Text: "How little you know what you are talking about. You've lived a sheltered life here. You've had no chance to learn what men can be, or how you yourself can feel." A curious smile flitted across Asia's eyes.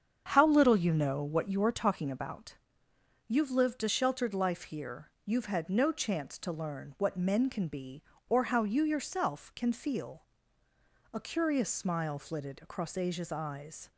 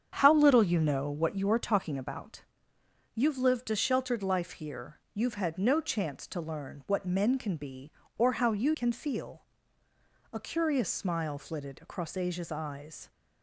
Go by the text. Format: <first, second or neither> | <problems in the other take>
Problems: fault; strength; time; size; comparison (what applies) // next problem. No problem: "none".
first | starts louder than the rest; strong; until 1.1 s; 8 dB; strong in the first // skips "yourself"; at 8.7 s